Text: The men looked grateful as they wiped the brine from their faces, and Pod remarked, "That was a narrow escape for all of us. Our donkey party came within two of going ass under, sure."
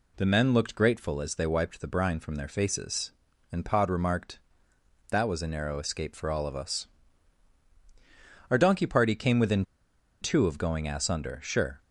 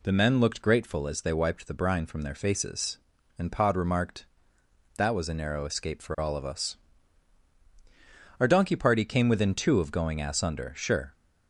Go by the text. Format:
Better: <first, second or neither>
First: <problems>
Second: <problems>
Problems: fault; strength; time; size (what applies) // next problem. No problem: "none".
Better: second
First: pauses between "within" and "two"; noticeable; at 9.6 s; 0.57 s long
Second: none